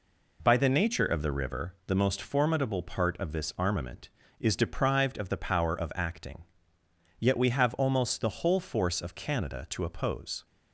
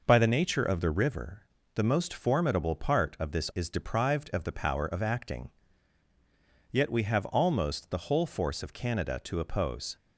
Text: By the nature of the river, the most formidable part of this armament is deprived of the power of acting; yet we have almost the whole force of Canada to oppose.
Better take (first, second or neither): first